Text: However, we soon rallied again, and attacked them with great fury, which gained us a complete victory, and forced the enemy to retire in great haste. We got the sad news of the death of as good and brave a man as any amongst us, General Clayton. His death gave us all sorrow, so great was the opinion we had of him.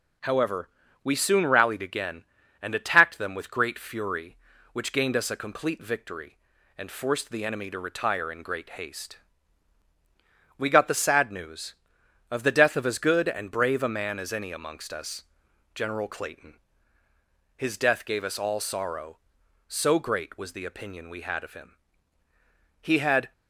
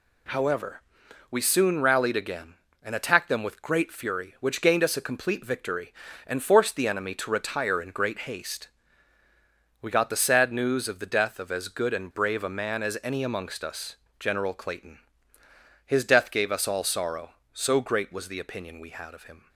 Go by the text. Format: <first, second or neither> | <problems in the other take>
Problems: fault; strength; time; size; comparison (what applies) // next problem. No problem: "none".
second | goes on to say "He had"; from 22.8 s on; 0.52 s long